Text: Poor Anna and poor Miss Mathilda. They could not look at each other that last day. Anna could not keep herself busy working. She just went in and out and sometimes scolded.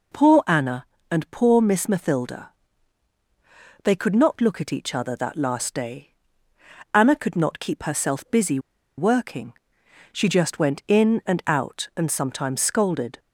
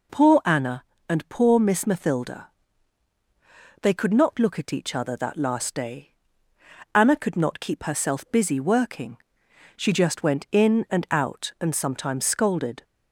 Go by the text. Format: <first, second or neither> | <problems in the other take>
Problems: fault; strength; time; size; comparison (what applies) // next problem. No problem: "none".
second | pauses between "busy" and "working"; at 8.5 s; 0.39 s long